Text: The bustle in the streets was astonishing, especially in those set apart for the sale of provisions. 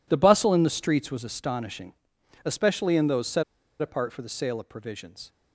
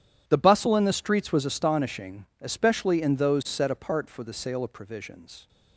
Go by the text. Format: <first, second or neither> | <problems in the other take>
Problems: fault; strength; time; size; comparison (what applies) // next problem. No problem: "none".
second | pauses between "set" and "apart"; at 3.4 s; 0.37 s long